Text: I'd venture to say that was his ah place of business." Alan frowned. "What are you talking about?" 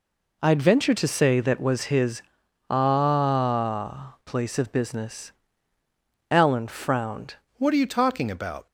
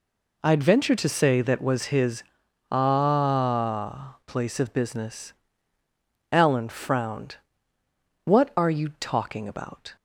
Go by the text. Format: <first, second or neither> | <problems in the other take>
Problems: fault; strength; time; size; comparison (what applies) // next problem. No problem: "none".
second | pauses between "his" and "ah"; noticeable; at 2.2 s; 0.48 s long; noticeable in the second // changes voice at "What"; from 7.5 s on; 1.1 s long